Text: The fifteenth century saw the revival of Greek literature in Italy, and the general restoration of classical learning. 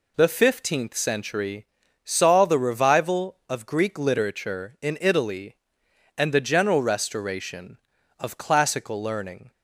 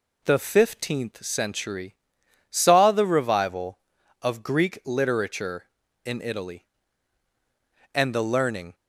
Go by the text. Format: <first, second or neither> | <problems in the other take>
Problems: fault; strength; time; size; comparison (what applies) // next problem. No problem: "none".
first | pauses between "century" and "saw"; noticeable; at 1.9 s; 0.56 s long; also in the first // skips "general restoration of classical"; at 8.2 s